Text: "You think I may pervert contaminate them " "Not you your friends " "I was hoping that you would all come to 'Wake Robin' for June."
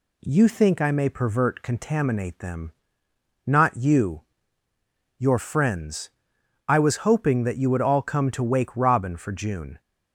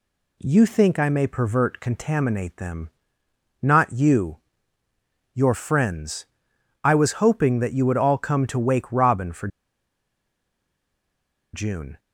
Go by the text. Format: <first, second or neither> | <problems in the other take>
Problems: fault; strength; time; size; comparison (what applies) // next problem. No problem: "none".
first | pauses between "you" and "your"; noticeable; at 4.3 s; 0.96 s long; noticeable in the first // pauses between "for" and "June"; strong; at 9.4 s; 2.0 s long